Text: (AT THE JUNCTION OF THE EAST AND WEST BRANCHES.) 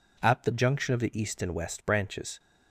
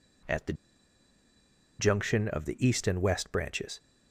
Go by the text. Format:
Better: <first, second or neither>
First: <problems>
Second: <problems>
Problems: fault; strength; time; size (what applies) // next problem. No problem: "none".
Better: first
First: none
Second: pauses between "THE" and "JUNCTION"; strong; at 0.5 s; 1.2 s long